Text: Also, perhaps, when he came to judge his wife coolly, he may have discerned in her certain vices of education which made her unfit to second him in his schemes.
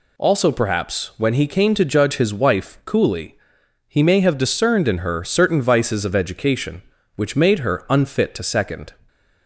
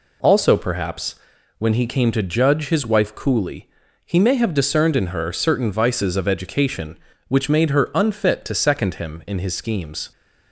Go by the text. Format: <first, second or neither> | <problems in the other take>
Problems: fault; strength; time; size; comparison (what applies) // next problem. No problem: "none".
second | stops before "him in his schemes"; at 9.0 s